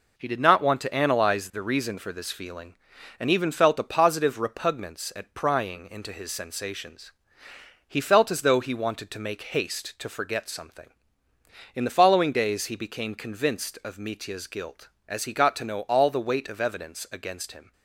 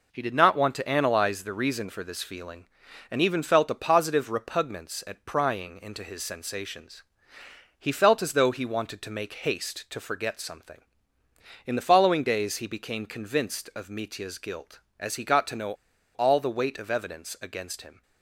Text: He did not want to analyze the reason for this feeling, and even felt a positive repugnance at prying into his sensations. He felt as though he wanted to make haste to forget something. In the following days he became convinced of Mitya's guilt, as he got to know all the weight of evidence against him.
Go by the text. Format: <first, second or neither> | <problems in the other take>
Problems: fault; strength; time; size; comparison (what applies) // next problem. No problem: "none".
first | pauses between "know" and "all"; at 15.7 s; 0.43 s long